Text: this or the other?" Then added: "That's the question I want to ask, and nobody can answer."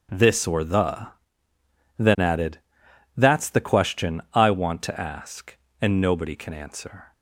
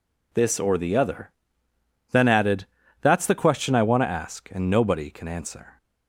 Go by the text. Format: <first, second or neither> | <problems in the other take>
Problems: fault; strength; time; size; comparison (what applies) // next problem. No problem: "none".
second | starts louder than the rest; strong; until 2.0 s; 7.5 dB // skips "other"; at 1.5 s